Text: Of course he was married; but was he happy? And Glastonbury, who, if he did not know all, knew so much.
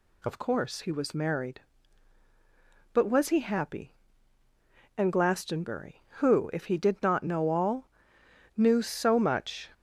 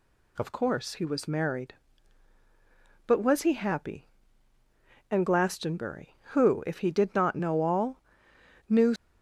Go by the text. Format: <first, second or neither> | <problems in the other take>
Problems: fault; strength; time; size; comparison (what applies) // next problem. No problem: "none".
first | stops before "so much"; at 8.9 s